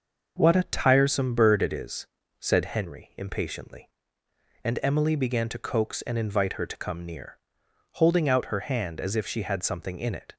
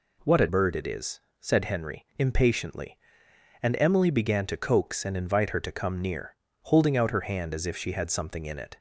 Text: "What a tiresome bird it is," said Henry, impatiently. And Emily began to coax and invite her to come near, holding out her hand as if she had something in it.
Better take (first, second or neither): first